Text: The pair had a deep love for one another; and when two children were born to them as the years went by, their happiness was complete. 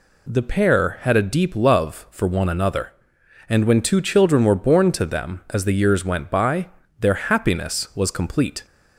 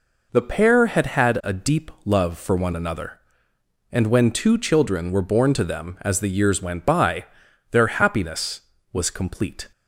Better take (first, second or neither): first